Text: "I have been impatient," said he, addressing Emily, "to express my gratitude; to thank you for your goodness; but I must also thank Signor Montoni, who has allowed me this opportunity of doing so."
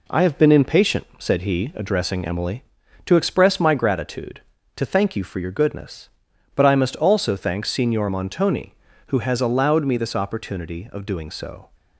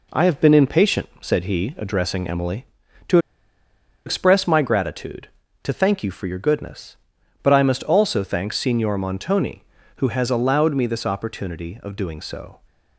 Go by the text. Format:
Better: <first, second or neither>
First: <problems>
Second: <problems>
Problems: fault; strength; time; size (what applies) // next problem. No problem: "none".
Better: first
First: none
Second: pauses between "to" and "express"; noticeable; at 3.1 s; 0.87 s long